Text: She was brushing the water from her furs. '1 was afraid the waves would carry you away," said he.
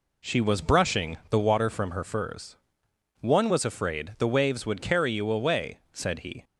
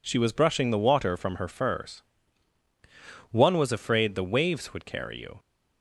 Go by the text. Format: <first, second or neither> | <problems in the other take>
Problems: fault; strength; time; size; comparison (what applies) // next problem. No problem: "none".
first | stops before "away said he"; at 5.3 s